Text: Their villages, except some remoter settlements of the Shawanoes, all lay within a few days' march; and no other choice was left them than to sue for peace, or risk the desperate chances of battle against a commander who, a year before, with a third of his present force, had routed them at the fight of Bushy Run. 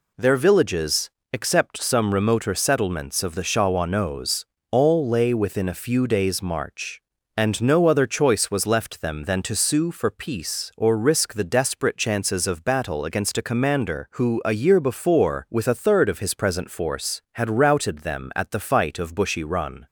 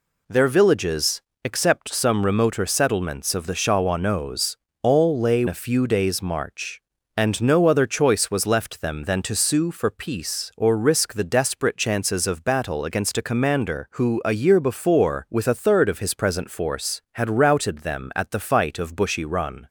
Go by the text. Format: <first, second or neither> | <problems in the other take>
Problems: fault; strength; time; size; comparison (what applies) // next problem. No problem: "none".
first | skips "within"; at 5.4 s